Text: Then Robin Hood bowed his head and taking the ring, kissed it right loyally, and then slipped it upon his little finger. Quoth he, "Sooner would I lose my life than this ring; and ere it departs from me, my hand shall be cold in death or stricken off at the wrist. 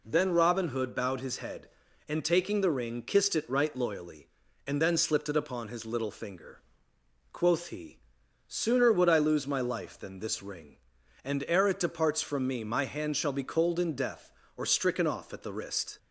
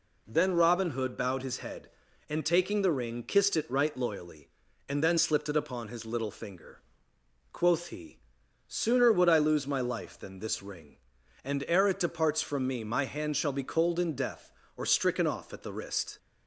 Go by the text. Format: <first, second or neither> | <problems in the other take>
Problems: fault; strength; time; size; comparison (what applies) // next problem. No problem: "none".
neither | none